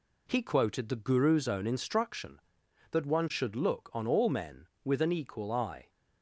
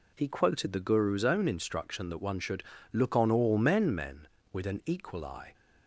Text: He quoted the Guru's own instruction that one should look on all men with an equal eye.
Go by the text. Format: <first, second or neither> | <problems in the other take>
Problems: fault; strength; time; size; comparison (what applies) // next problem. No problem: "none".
first | pauses between "should" and "look"; slight; at 2.6 s; 0.28 s long // says "men" twice; at 3.9 s